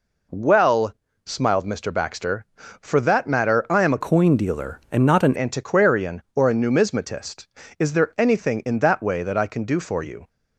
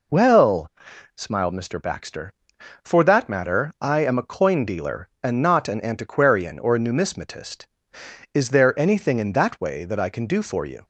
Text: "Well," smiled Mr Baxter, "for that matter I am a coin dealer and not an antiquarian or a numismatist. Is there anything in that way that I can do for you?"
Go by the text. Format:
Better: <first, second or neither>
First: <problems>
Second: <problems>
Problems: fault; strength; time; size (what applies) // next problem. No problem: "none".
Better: second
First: changes voice from "coin" to "an"; from 4.0 to 5.3 s; 1.3 s long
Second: none